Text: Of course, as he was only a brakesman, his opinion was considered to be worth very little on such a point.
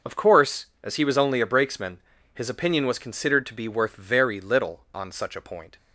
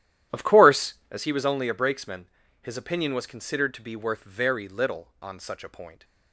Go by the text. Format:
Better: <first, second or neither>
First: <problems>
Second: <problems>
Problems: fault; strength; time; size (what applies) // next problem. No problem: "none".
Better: first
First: none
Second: starts louder than the rest; strong; until 1.2 s; 11.5 dB